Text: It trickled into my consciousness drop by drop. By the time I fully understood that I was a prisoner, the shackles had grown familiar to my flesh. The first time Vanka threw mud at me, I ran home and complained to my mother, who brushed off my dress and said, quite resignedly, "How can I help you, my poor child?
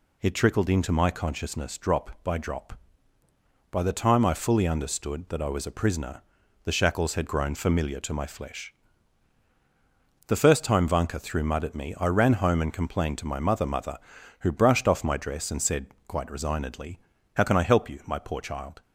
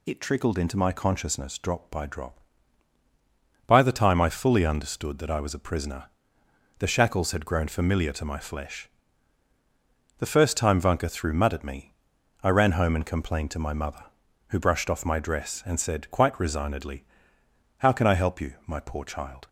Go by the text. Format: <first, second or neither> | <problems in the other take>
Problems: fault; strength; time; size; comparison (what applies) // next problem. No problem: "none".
second | says "mother" twice; at 13.6 s